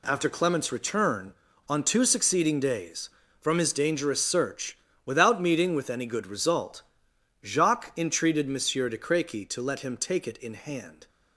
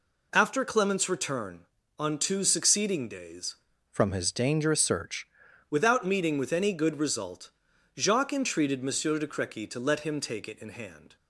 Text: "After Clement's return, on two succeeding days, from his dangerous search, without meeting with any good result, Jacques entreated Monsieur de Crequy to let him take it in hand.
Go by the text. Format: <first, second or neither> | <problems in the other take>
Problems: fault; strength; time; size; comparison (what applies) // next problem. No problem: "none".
first | changes voice from "from" to "search"; from 3.8 to 5.2 s; 1.4 s long